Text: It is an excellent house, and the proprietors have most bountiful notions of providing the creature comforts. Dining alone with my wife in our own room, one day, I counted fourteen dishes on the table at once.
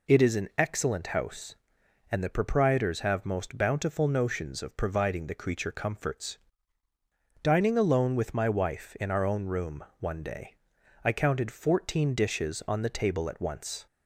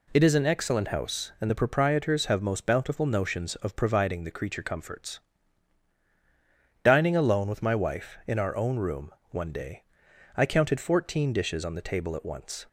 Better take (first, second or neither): neither